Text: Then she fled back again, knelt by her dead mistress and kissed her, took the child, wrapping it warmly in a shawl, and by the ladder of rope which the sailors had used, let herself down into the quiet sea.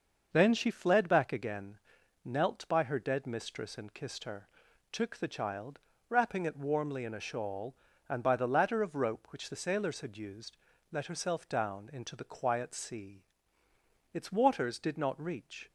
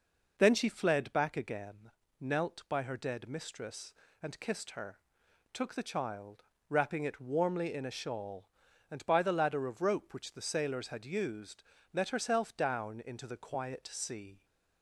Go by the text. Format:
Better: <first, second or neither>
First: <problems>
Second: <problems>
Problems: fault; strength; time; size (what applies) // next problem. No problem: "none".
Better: second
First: starts louder than the rest; noticeable; until 1.3 s; 6 dB // goes on to say "Its waters did not reach"; from 14.1 s on; 1.5 s long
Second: none